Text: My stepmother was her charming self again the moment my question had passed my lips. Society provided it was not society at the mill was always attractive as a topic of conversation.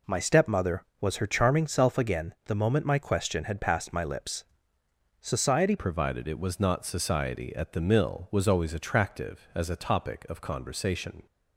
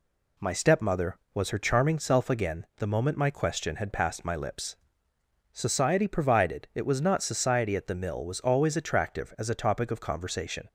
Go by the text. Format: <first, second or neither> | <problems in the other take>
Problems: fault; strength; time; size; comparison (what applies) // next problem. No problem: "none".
second | changes voice at "provided"; from 5.7 s on; 5.5 s long